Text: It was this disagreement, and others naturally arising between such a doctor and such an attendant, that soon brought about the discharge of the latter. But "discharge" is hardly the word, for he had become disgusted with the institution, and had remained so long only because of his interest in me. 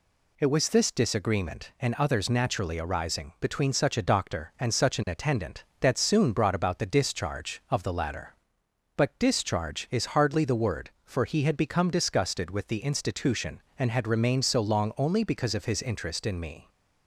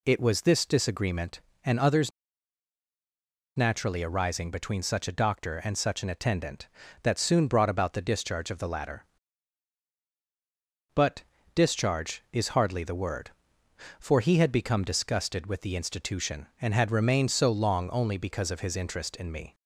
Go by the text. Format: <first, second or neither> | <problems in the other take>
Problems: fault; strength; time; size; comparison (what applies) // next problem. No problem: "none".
first | pauses between "others" and "naturally"; strong; at 2.1 s; 1.4 s long // pauses between "But" and "discharge"; slight; at 11.2 s; 0.32 s long